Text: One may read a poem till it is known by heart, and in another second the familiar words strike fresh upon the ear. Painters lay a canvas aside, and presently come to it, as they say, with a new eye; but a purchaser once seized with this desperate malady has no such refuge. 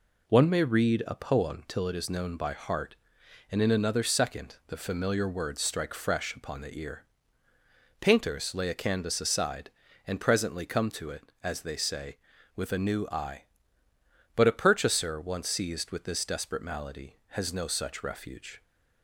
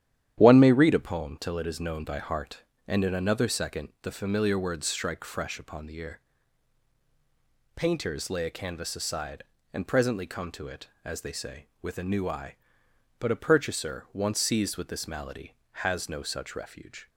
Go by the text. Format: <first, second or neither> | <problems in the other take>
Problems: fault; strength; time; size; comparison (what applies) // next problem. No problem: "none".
first | starts louder than the rest; strong; until 1.4 s; 10.5 dB // skips "desperate"; at 15.0 s